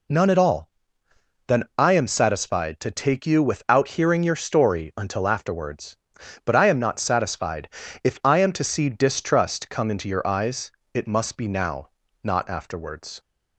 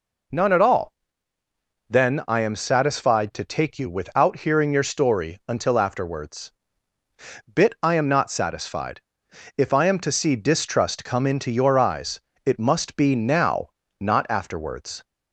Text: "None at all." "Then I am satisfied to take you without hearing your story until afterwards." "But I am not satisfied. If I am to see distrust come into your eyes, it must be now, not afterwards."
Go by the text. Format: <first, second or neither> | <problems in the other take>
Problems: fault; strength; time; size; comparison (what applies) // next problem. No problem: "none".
first | says "Bit" for "But"; at 7.5 s